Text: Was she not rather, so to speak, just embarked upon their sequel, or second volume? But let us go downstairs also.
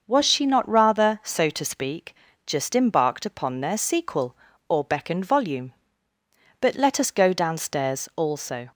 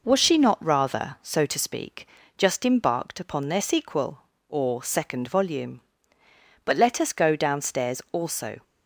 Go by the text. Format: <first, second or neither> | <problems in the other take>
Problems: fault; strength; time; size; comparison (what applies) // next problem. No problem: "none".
second | starts louder than the rest; noticeable; until 1.0 s; 6 dB // says "beckoned" for "second"; at 4.8 s